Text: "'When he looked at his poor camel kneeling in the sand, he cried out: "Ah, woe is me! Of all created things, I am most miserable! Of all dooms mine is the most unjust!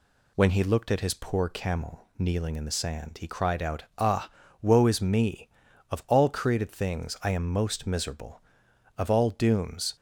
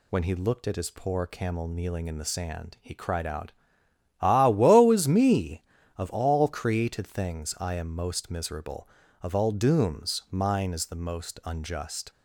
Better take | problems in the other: second | stops before "mine is the most unjust"; at 9.9 s

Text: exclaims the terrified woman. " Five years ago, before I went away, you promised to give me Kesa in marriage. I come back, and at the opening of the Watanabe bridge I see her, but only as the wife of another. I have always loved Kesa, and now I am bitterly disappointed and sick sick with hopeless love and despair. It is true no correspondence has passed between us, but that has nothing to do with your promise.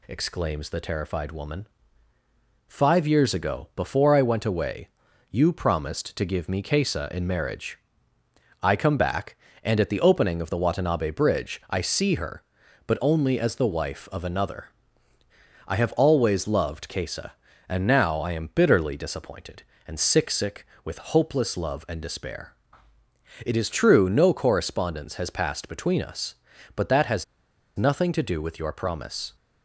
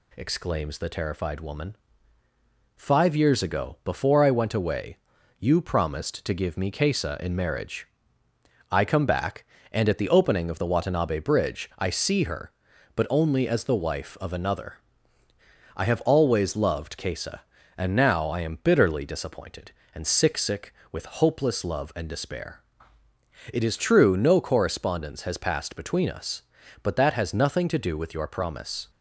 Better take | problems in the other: second | pauses between "has" and "nothing"; noticeable; at 27.2 s; 0.52 s long

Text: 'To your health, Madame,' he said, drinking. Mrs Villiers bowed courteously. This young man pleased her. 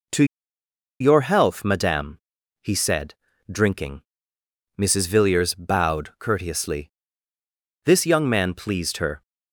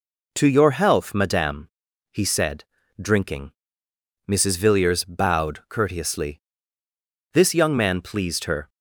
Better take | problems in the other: second | pauses between "To" and "your"; noticeable; at 0.2 s; 0.76 s long

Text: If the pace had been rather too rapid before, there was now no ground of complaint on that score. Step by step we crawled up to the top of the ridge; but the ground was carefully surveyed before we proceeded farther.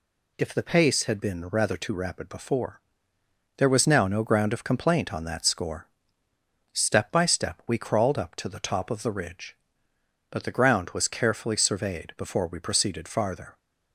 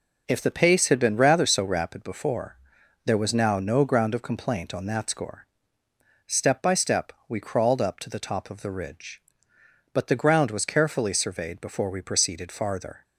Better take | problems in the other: first | says "so" for "too"; at 1.4 s // pauses between "step" and "we"; slight; at 7.1 s; 0.16 s long

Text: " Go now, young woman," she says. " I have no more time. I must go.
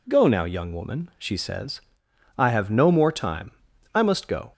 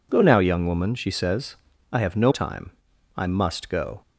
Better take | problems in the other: first | skips "more"; at 2.3 s

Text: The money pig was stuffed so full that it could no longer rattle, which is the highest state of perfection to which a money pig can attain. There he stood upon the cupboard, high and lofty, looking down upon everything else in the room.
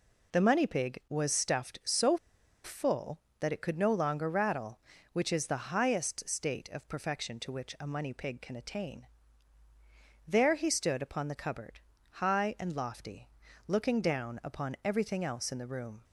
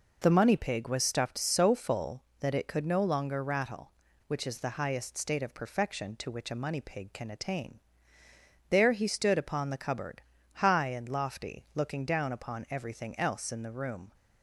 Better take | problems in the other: second | pauses between "so" and "full"; noticeable; at 2.1 s; 0.46 s long

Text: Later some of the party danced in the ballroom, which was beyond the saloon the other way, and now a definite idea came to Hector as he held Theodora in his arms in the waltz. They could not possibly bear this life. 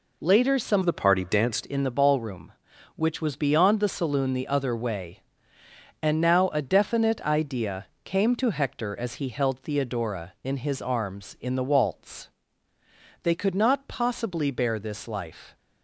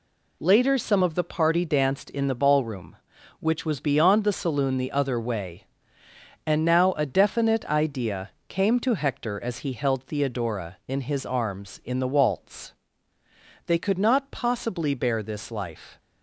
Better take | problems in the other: second | changes voice from "of" to "danced"; from 0.8 to 1.6 s; 0.8 s long // pauses between "idea" and "came"; slight; at 7.8 s; 0.18 s long; slight in the second

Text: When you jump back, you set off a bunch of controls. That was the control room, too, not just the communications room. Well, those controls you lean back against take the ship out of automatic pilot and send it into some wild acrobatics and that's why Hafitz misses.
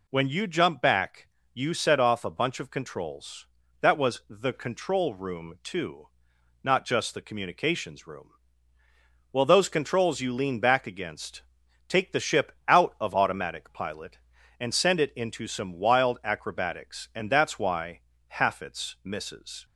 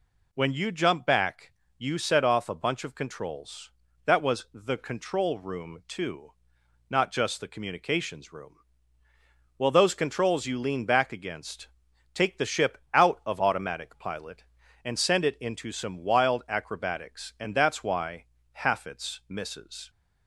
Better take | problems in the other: neither | pauses between "against" and "take"; noticeable; the same in both // pauses between "ship" and "out"; slight; the same in both // pauses between "why" and "Hafitz"; slight; the same in both

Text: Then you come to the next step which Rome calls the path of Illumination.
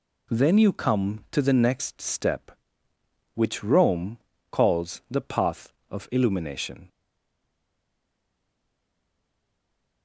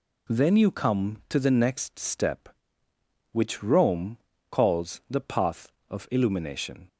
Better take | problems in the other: second | pauses between "Rome" and "calls"; slight; at 4.1 s; 0.32 s long; slight in the second // stays silent after the last word; strong; from 6.8 s on; 3.2 s long

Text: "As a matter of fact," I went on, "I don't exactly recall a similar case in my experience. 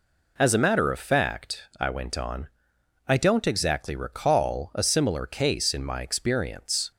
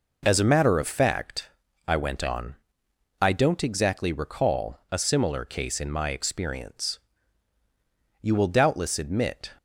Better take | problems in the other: first | goes on to say "You will doubtless admit"; noticeable; from 8.2 s on; 1.3 s long

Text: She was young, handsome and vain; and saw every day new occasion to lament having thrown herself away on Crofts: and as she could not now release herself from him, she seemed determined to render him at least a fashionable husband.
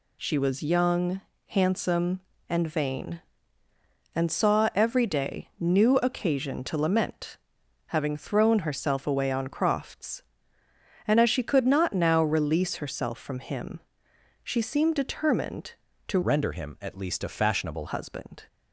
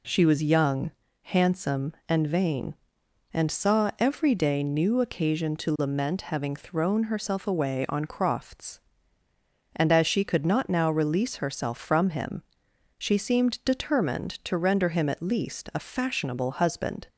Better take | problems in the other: second | pauses between "lament" and "having"; noticeable; at 7.3 s; 0.48 s long // changes voice from "render" to "fashionable"; from 16.2 to 17.8 s; 1.6 s long

